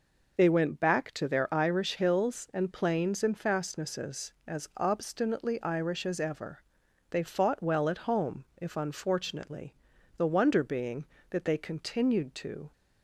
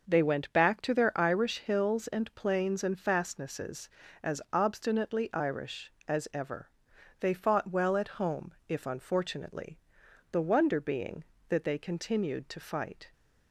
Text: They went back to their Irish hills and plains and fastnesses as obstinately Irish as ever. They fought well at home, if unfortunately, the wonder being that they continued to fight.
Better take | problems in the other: second | stops before "fight"; at 12.7 s

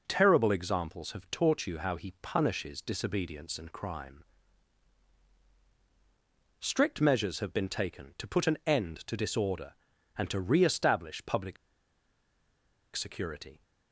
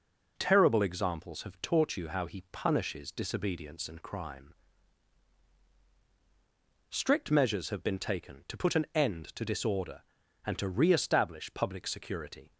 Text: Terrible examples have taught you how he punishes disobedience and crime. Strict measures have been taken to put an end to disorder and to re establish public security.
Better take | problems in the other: second | pauses between "public" and "security"; strong; at 11.5 s; 1.4 s long

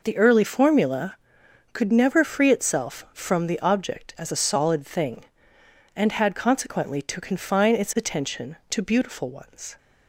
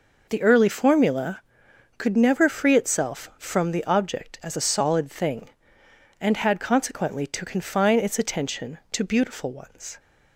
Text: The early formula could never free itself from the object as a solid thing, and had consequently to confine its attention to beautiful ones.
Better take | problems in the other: neither | none

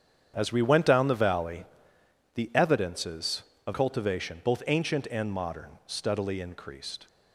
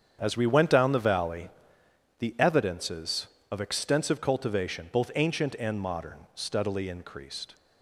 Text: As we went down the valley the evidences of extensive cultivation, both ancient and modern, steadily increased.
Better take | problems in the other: second | starts louder than the rest; strong; until 1.3 s; 8.5 dB; strong in the second // pauses between "valley" and "the"; noticeable; at 1.6 s; 0.70 s long; noticeable in the second // skips "extensive"; at 3.7 s

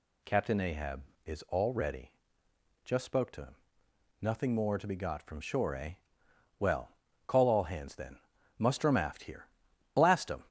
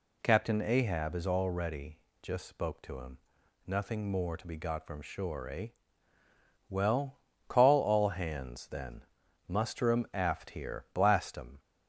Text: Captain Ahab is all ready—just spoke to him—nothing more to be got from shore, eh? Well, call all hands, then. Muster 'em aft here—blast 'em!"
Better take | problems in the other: neither | none

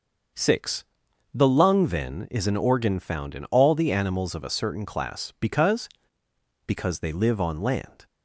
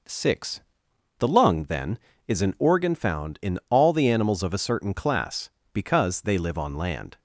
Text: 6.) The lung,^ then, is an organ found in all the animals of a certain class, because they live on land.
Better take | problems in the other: second | starts louder than the rest; until 1.8 s; 6 dB // says "because" twice; at 6.6 s

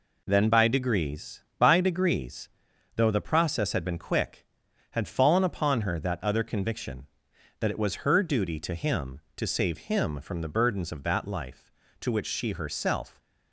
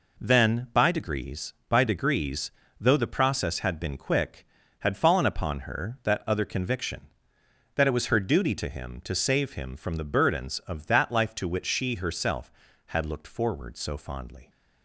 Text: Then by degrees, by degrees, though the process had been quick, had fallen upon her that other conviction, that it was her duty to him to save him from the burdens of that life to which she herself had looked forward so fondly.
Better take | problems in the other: second | stops before "had looked forward so fondly"; at 13.1 s

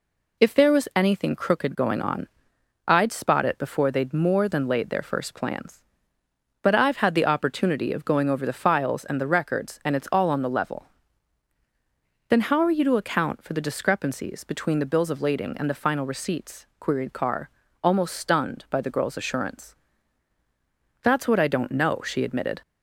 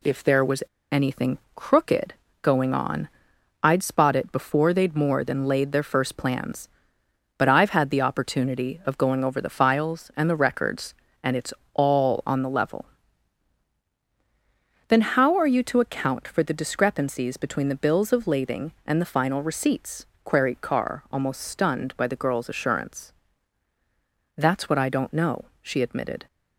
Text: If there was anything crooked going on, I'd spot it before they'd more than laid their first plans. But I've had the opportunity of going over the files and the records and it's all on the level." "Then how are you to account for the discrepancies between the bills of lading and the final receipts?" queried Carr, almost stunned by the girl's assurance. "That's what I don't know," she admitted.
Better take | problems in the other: first | pauses between "was" and "anything"; slight; at 0.6 s; 0.27 s long // pauses between "anything" and "crooked"; slight; at 1.3 s; 0.16 s long // pauses between "crooked" and "going"; slight; at 2.1 s; 0.26 s long // pauses between "it's" and "all"; slight; at 11.5 s; 0.18 s long

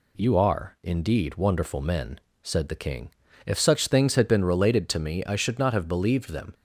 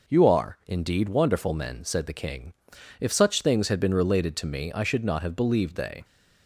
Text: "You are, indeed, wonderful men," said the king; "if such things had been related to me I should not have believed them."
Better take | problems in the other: first | says "they" for "them"; at 5.7 s

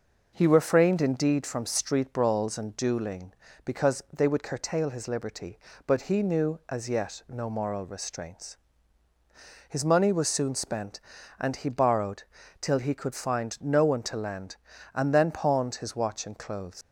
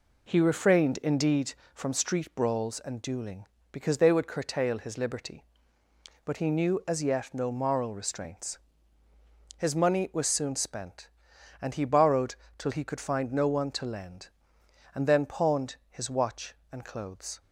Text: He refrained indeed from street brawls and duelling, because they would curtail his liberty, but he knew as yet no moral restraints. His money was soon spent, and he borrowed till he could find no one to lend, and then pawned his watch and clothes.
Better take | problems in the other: second | pauses between "borrowed" and "till"; slight; at 12.2 s; 0.36 s long; slight in the second // leaves "clothes" unfinished; at 16.8 s; 110 ms

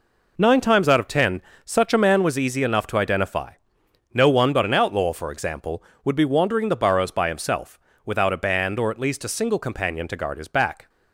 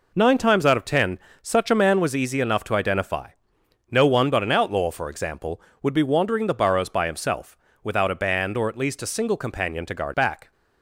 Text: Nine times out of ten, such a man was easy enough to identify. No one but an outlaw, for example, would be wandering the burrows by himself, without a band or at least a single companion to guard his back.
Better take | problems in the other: first | skips "his"; at 10.1 s

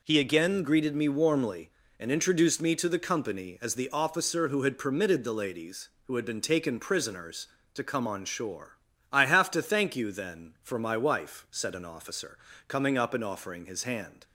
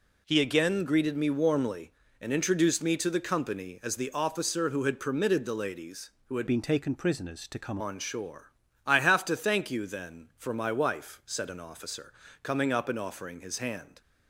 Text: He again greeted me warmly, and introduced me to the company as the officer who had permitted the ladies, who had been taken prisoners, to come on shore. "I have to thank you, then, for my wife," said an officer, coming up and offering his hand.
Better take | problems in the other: first | changes voice from "been" to "come"; from 6.4 to 7.7 s; 1.3 s long

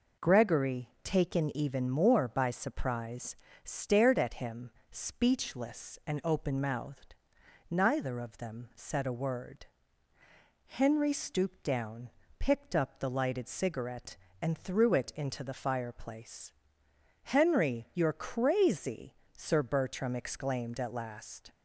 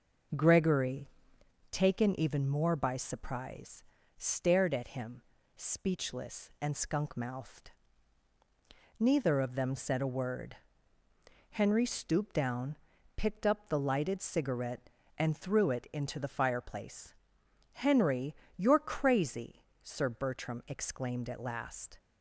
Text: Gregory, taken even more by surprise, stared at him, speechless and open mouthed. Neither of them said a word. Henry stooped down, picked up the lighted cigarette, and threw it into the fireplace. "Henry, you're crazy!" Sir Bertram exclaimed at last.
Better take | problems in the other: first | says "skunk" for "open"; at 6.7 s

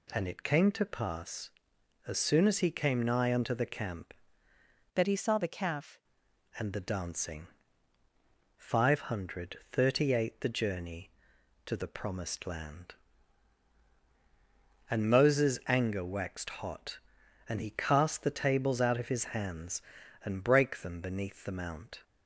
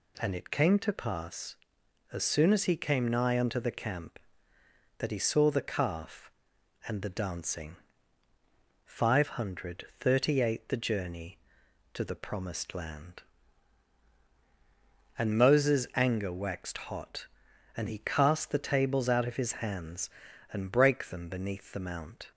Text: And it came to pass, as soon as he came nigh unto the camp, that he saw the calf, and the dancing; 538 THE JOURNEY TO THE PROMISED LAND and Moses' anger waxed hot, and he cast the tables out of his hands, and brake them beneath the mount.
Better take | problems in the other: second | changes voice from "that" to "calf"; from 4.9 to 5.9 s; 1.0 s long

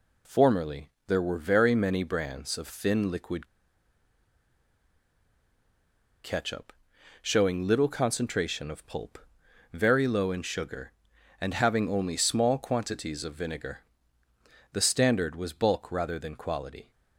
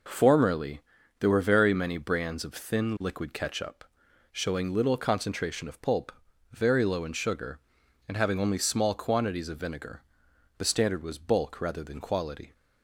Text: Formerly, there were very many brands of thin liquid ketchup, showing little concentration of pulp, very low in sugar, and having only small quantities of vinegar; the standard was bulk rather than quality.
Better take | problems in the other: second | pauses between "liquid" and "ketchup"; strong; at 3.4 s; 2.7 s long

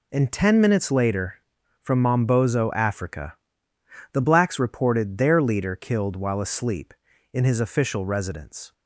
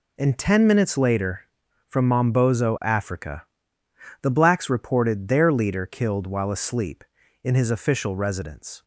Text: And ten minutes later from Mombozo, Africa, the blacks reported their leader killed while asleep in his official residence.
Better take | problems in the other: neither | none

